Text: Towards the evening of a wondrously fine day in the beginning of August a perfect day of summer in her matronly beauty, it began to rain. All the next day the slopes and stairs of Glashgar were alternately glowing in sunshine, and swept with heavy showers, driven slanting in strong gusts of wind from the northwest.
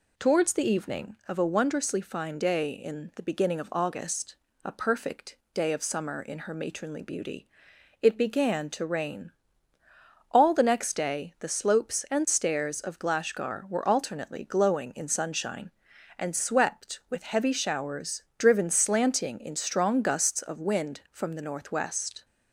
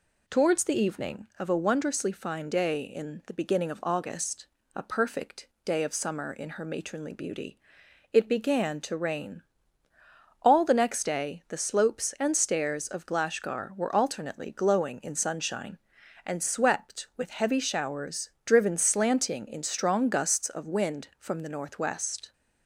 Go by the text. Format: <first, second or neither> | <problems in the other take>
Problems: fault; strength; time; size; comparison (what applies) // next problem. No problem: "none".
neither | pauses between "August" and "a"; slight; the same in both // pauses between "perfect" and "day"; slight; the same in both